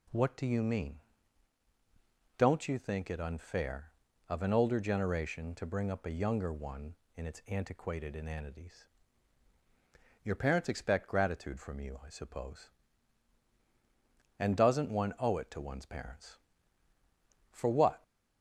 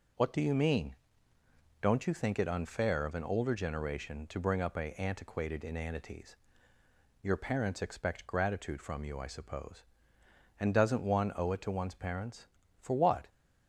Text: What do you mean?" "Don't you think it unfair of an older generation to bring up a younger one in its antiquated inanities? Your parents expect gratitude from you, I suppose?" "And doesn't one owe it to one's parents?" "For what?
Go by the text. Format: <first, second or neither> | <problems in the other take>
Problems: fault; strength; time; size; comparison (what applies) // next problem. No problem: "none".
first | skips "younger one in its"; at 4.9 s